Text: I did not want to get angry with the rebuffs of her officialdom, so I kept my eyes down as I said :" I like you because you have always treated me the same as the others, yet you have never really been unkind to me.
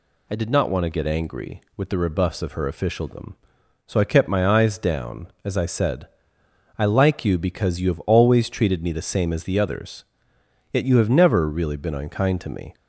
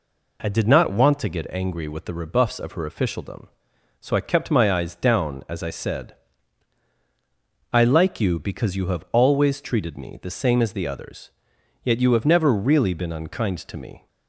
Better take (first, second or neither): neither